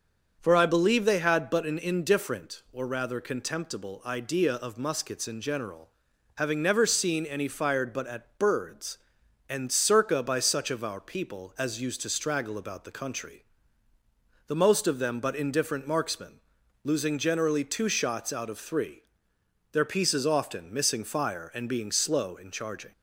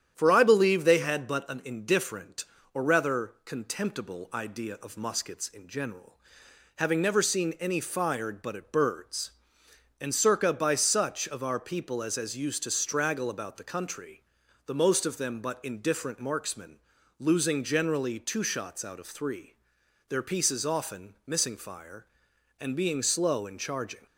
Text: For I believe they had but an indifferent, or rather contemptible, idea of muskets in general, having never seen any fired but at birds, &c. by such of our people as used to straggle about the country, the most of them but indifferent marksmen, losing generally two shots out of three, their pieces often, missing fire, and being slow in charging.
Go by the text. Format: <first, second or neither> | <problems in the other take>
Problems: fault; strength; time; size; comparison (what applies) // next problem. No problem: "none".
first | starts louder than the rest; strong; until 1.1 s; 9.5 dB; also in the first // says "as" twice; at 12.1 s